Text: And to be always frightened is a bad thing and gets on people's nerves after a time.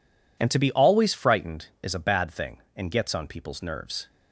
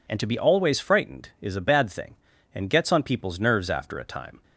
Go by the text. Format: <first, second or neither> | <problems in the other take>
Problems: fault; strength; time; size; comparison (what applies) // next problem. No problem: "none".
second | stops before "after a time"; at 4.0 s